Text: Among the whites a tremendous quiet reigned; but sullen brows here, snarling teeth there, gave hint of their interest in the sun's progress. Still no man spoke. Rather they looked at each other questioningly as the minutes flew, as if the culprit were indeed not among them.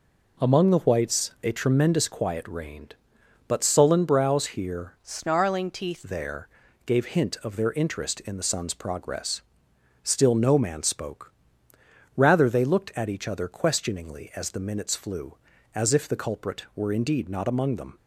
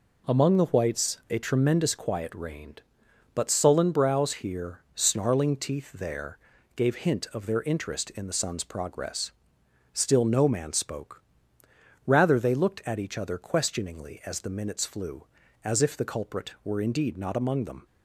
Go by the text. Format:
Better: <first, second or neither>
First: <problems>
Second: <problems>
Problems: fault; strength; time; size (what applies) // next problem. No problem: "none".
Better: second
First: changes voice from "snarling" to "teeth"; from 5.0 to 6.0 s; 1.0 s long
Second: none